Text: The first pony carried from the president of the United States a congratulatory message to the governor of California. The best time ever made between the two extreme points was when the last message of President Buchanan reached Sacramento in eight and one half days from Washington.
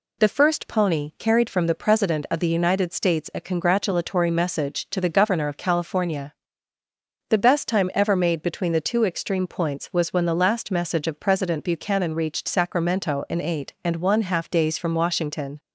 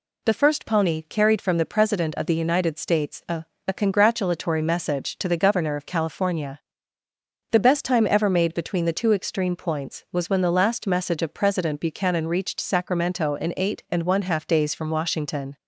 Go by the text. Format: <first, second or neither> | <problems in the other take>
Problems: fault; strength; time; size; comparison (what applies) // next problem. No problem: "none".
first | says "a" twice; at 3.6 s